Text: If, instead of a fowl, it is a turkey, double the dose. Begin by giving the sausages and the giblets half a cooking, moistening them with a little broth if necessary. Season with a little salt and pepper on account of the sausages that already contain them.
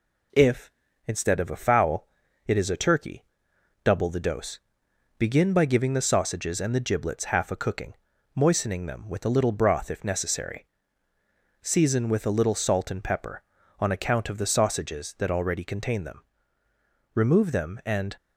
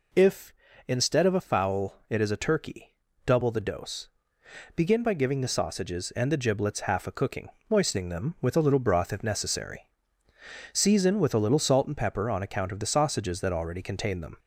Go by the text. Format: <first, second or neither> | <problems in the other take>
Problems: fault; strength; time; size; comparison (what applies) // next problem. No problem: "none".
second | goes on to say "Remove them and"; noticeable; from 17.1 s on; 1.0 s long